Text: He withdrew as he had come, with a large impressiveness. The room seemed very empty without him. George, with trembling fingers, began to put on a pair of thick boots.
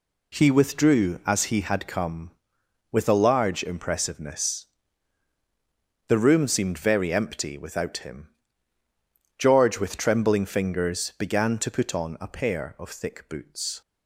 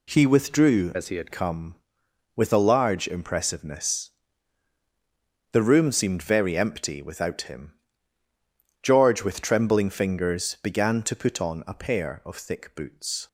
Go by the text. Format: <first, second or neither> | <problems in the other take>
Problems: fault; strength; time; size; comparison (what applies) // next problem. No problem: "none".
first | changes voice from "as" to "had"; from 0.9 to 1.3 s; 0.4 s long